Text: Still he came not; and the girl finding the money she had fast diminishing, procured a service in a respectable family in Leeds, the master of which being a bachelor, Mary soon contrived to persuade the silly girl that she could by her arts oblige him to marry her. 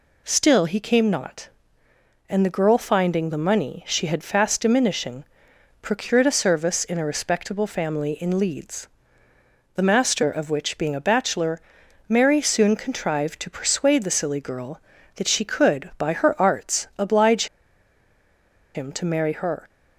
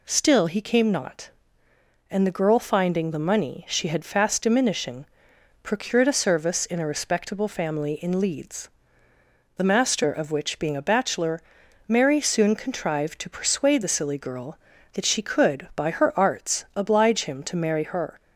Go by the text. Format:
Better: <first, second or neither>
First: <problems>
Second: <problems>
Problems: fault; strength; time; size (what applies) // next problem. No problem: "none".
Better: second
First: pauses between "oblige" and "him"; strong; at 17.4 s; 1.2 s long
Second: none